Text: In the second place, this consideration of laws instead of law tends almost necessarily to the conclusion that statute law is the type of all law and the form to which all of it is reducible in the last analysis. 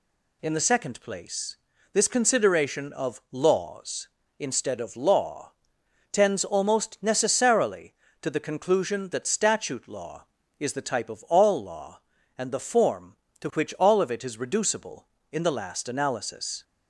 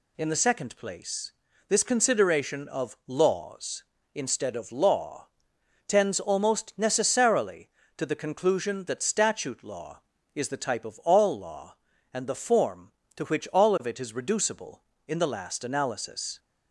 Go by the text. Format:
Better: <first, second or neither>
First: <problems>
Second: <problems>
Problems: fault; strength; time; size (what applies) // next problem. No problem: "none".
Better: neither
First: pauses between "law" and "tends"; noticeable; at 5.5 s; 0.60 s long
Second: pauses between "law" and "tends"; noticeable; at 5.2 s; 0.60 s long